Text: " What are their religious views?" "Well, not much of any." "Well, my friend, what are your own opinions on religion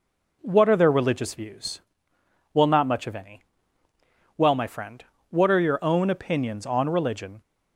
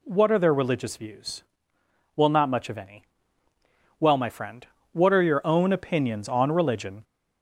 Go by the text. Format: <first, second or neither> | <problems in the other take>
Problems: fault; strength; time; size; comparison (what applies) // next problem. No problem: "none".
first | gets louder; slight; throughout; 2.5 dB